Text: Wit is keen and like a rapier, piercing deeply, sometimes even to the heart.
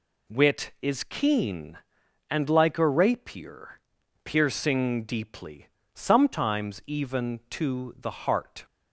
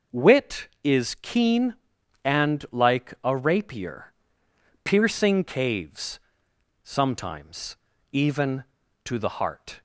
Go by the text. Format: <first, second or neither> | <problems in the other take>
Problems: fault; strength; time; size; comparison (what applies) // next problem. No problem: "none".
first | says "caves" for "deeply"; at 5.4 s // pauses between "sometimes" and "even"; slight; at 7.7 s; 0.34 s long